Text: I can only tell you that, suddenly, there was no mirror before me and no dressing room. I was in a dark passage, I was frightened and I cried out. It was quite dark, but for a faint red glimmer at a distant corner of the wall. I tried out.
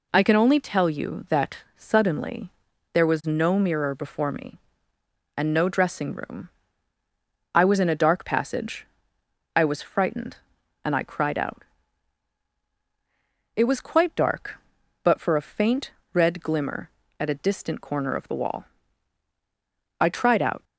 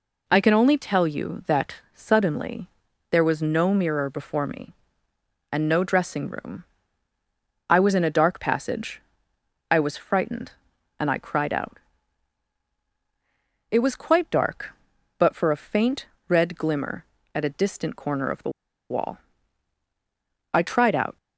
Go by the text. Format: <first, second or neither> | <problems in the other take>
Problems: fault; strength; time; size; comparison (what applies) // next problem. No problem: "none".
first | pauses between "faint" and "red"; slight; at 16.0 s; 0.20 s long; slight in the first // pauses between "the" and "wall"; at 18.5 s; 0.39 s long